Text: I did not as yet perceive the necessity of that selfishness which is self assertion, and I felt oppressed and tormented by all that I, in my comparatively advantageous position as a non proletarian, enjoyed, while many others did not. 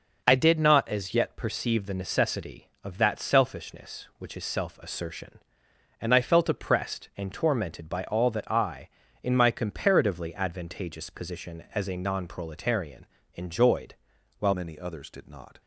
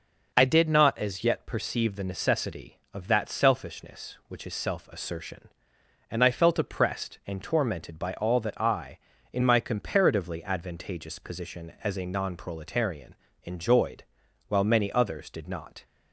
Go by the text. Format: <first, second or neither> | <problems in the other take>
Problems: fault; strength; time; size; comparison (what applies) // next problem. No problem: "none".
second | changes voice at "many"; from 14.5 s on; 1.1 s long